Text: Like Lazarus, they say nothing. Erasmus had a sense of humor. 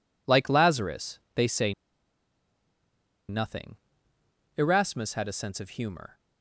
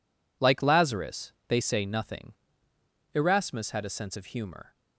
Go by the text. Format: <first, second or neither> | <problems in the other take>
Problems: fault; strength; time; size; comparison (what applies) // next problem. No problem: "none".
second | pauses between "say" and "nothing"; strong; at 1.7 s; 1.5 s long